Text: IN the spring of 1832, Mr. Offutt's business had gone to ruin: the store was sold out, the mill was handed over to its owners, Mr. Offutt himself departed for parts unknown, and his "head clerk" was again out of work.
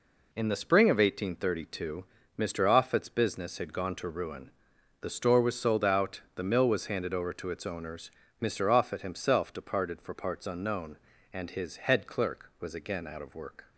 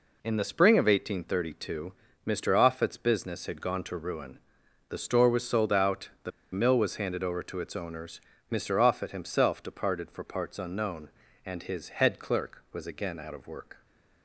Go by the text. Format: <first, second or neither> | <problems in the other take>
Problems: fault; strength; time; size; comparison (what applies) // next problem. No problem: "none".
first | pauses between "the" and "mill"; slight; at 6.3 s; 0.22 s long